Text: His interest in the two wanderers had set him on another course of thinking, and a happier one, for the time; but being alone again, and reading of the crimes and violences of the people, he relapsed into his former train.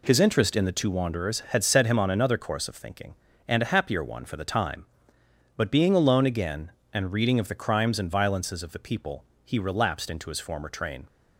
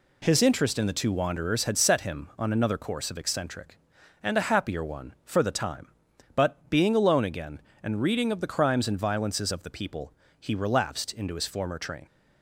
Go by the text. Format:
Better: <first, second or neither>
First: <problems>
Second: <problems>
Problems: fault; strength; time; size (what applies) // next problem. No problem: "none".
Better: first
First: none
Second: says "eccentric" for "thinking"; at 3.1 s